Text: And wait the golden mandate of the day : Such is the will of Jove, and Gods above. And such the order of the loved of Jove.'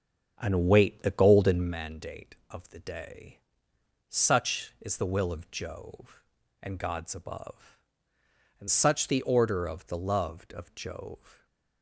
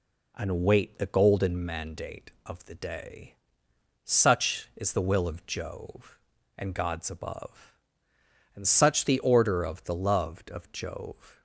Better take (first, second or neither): second